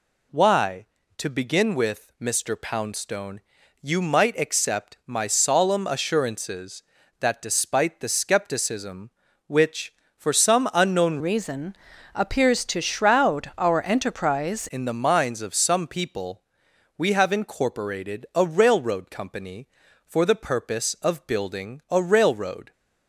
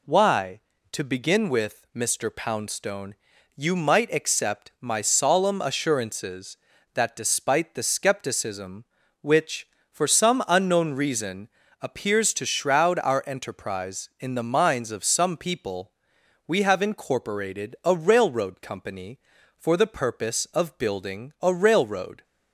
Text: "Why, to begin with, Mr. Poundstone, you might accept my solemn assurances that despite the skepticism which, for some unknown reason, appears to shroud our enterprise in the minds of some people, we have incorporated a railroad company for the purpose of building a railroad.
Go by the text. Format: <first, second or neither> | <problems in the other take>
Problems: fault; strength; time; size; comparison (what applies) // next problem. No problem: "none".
second | changes voice from "reason" to "enterprise"; from 11.1 to 14.6 s; 3.5 s long